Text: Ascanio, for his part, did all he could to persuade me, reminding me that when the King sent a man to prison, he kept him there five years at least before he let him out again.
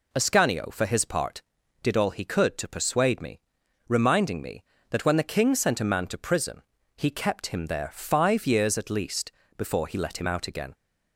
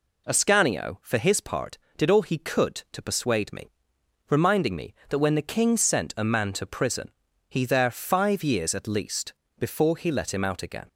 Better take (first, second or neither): first